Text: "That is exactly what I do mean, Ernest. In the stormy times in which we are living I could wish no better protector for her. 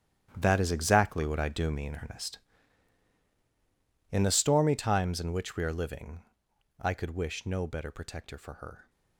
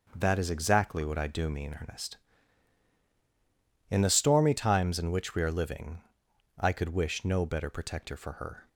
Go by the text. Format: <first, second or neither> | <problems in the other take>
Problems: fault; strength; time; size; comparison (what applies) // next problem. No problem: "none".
second | gets quieter; strong; throughout; 13.5 dB // starts louder than the rest; strong; until 1.3 s; 11 dB; also in the second // pauses between "living" and "I"; noticeable; at 6.2 s; 0.56 s long; noticeable in the second